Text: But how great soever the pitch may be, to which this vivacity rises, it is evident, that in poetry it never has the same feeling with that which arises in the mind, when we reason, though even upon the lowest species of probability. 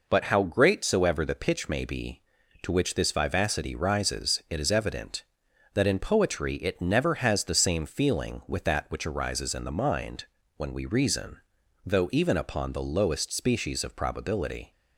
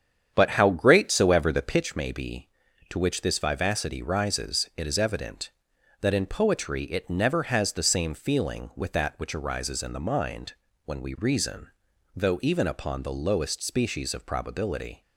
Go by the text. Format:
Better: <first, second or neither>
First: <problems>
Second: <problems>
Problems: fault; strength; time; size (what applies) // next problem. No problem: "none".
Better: first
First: none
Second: starts louder than the rest; strong; until 1.9 s; 8.5 dB